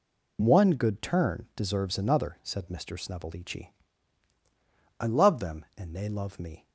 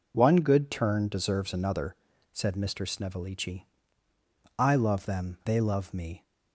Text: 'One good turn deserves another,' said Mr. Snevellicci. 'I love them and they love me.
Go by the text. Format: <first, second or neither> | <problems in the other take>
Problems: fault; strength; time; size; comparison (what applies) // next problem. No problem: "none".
first | skips "and"; at 5.4 s